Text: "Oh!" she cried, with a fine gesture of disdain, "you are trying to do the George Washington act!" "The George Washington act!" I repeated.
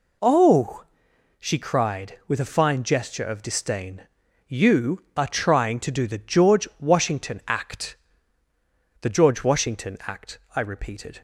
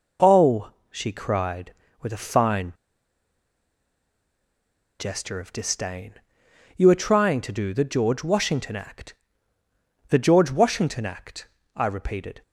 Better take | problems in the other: first | pauses between "fine" and "gesture"; strong; at 2.7 s; 2.2 s long

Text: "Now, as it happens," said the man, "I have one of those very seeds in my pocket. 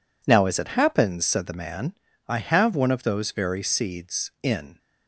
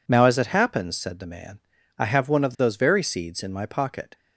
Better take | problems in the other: second | stops before "my pocket"; at 4.7 s

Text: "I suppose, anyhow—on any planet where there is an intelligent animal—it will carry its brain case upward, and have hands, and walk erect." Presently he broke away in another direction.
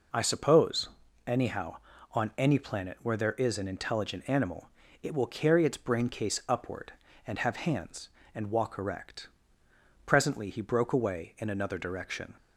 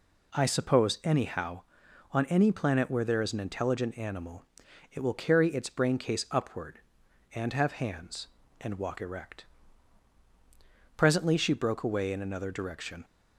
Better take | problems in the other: first | says "she" for "he"; at 11.3 s

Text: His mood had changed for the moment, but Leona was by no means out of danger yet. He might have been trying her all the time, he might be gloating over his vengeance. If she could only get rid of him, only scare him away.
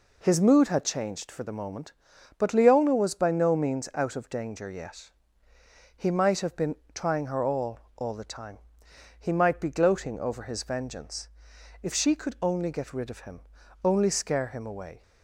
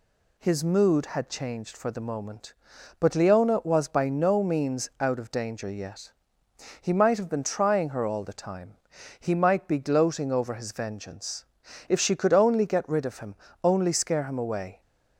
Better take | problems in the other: second | pauses between "been" and "trying"; slight; at 6.7 s; 0.18 s long // says "all" twice; at 7.9 s

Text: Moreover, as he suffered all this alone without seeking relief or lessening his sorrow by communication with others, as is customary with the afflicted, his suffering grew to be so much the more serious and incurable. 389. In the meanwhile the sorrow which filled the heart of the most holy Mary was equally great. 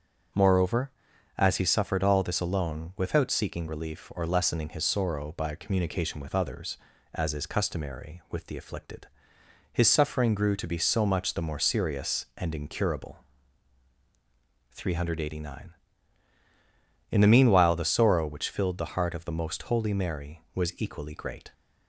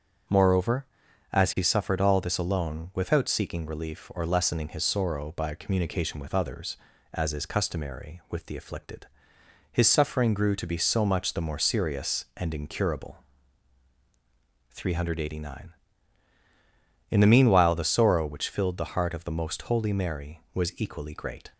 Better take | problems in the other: neither | none

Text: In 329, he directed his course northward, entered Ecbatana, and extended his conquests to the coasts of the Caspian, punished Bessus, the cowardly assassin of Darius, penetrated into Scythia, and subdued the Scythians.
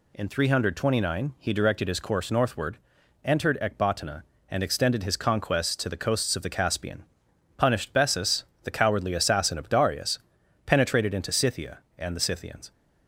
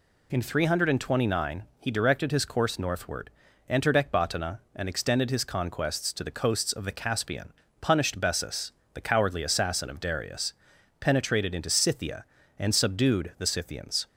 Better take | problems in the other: second | skips "subdued"; at 12.1 s

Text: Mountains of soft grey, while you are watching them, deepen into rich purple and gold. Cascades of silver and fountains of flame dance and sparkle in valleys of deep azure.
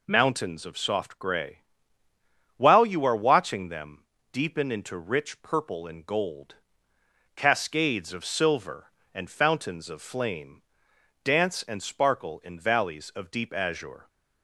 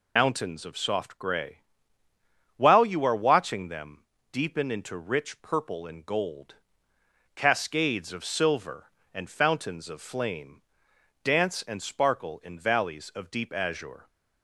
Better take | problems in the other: first | loses the start of "Mountains"; at 0.1 s; 90 ms // pauses between "flame" and "dance"; noticeable; at 10.6 s; 0.62 s long; noticeable in the first

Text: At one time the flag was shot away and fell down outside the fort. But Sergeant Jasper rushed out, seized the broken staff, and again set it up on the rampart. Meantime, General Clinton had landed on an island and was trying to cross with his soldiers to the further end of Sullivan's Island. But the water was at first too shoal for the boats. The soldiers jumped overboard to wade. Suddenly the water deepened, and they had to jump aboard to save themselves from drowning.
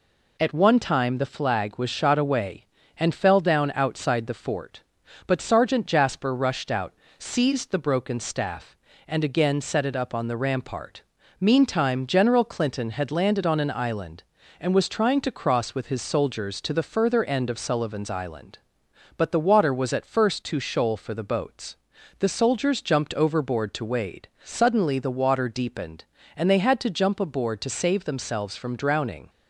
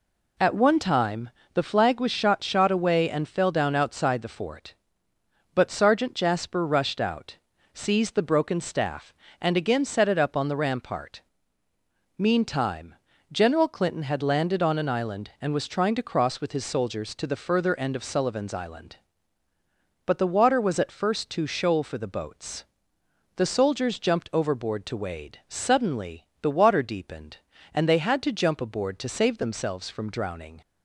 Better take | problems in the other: first | pauses between "time" and "the"; slight; at 1.3 s; 0.24 s long // says "shot" twice; at 2.4 s // pauses between "Suddenly" and "the"; slight; at 26.2 s; 0.16 s long

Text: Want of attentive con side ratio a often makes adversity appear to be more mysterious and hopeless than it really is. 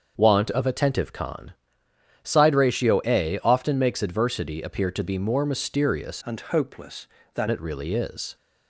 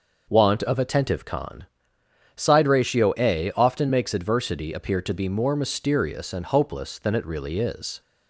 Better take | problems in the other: second | starts louder than the rest; until 1.2 s; 6.5 dB // pauses between "con" and "side"; noticeable; at 1.5 s; 0.72 s long; noticeable in the second // changes voice from "and" to "than"; from 6.2 to 7.4 s; 1.2 s long

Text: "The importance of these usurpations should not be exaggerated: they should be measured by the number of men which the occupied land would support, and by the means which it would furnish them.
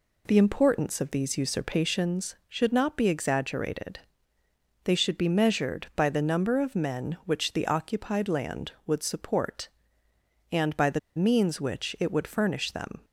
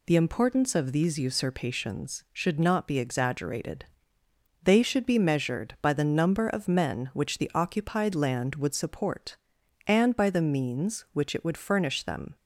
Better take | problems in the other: second | pauses between "the" and "means"; slight; at 10.9 s; 0.16 s long

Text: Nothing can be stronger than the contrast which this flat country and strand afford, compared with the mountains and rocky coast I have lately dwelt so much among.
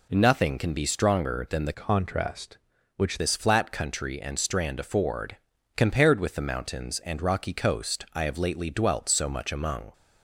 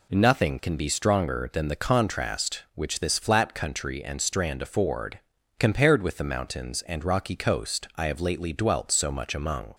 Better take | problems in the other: second | changes voice from "contrast" to "which"; from 1.7 to 3.1 s; 1.4 s long

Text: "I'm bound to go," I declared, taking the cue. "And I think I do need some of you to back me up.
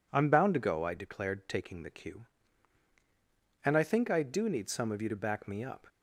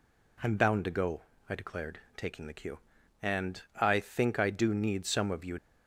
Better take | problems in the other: first | stops before "to back me up"; at 5.5 s

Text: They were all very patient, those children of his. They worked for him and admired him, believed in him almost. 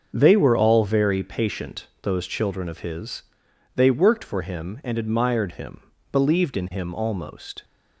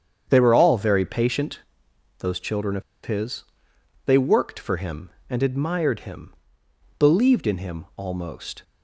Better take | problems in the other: first | starts louder than the rest; strong; until 1.2 s; 8 dB; also in the first // pauses between "of" and "his"; slight; at 2.8 s; 0.22 s long

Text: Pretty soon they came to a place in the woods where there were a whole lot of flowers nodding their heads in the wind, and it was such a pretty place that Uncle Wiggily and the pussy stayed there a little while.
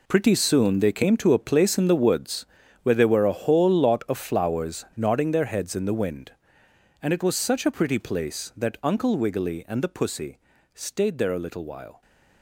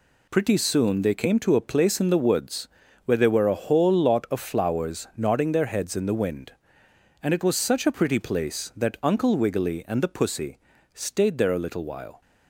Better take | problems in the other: second | gets quieter; strong; throughout; 12 dB // pauses between "woods" and "where"; at 2.4 s; 0.38 s long; also in the second // pauses between "pussy" and "stayed"; slight; at 10.3 s; 0.36 s long; slight in the second

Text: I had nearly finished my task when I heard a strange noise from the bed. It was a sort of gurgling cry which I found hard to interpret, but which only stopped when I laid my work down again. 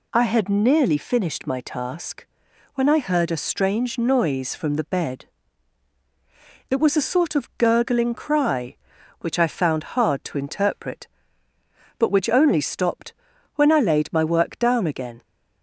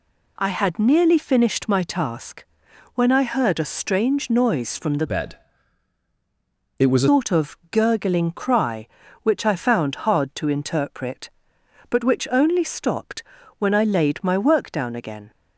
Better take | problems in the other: first | pauses between "task" and "when"; noticeable; at 2.4 s; 0.50 s long; noticeable in the first // changes voice from "bed" to "a"; from 5.0 to 7.0 s; 2.0 s long // pauses between "stopped" and "when"; at 13.2 s; 0.38 s long; also in the first

